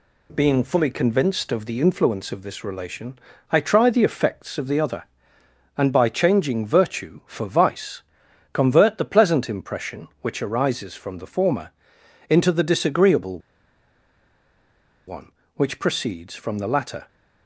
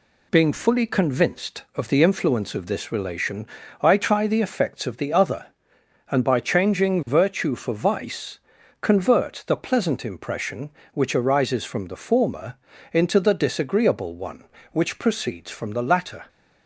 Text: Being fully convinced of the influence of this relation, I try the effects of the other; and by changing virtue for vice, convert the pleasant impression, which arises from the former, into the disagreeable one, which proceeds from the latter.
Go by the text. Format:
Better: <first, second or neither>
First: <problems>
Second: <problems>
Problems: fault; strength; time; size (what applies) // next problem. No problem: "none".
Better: second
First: pauses between "disagreeable" and "one"; strong; at 13.3 s; 1.6 s long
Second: none